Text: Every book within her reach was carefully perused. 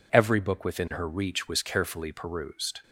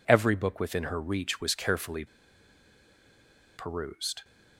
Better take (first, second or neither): first